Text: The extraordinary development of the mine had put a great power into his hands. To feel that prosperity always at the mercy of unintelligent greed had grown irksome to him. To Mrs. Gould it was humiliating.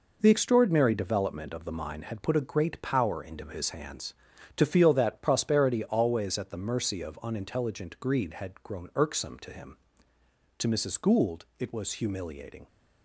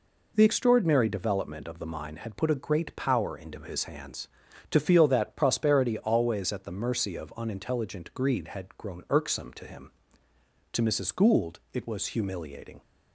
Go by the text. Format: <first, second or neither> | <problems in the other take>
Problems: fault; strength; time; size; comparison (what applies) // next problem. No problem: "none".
second | gets quieter; strong; throughout; 8 dB